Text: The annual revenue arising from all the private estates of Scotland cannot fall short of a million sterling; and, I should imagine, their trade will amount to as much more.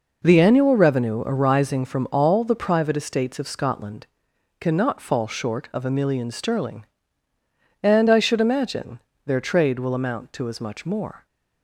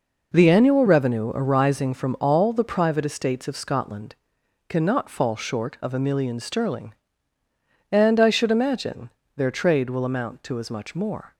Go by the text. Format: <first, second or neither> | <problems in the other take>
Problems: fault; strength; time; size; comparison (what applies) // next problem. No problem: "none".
neither | pauses between "Scotland" and "cannot"; noticeable; the same in both